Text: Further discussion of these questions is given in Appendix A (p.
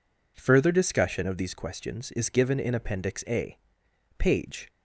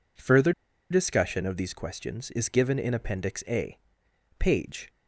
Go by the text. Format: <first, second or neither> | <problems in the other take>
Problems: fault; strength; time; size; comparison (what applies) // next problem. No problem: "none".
first | pauses between "Further" and "discussion"; at 0.5 s; 0.39 s long